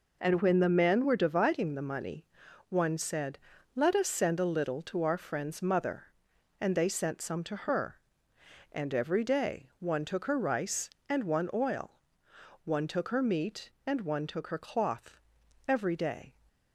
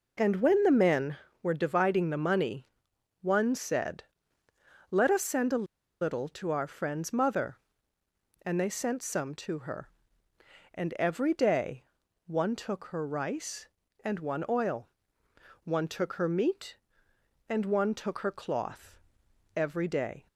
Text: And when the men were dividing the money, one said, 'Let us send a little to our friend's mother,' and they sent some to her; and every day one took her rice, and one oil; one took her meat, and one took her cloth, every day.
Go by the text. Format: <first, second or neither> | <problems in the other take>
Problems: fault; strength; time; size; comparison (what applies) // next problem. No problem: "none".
first | pauses between "a" and "little"; at 5.6 s; 0.36 s long // pauses between "day" and "one"; at 11.8 s; 0.42 s long